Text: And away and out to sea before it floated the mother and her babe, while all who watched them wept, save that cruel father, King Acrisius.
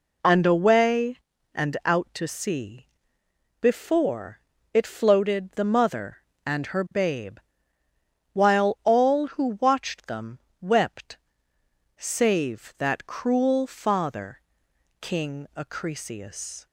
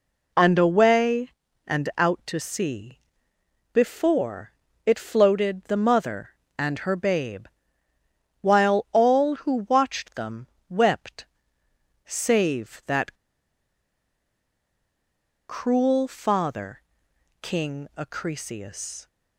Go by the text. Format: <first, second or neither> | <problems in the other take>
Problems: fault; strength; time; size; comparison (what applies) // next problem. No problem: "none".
first | pauses between "sea" and "before"; noticeable; at 2.9 s; 0.76 s long; noticeable in the first // pauses between "before" and "it"; slight; at 4.5 s; 0.34 s long; slight in the first // pauses between "them" and "wept"; slight; at 10.4 s; 0.24 s long; slight in the first // pauses between "that" and "cruel"; strong; at 13.1 s; 2.3 s long